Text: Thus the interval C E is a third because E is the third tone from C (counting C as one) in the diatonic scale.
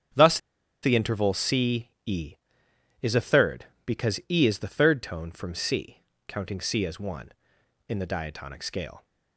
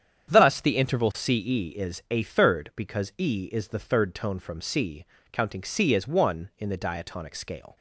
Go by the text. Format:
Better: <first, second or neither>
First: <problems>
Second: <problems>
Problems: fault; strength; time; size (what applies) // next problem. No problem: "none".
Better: second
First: starts louder than the rest; strong; until 1.5 s; 8.5 dB // pauses between "Thus" and "the"; at 0.3 s; 0.45 s long // pauses between "C" and "E"; slight; at 1.8 s; 0.18 s long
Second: starts louder than the rest; strong; until 1.3 s; 8.5 dB